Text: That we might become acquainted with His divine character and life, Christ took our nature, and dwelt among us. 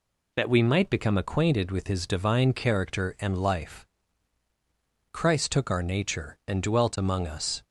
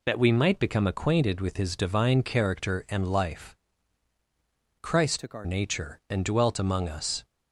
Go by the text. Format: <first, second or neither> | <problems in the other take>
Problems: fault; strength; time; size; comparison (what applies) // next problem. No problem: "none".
first | changes voice from "took" to "our"; from 5.1 to 5.4 s; 0.3 s long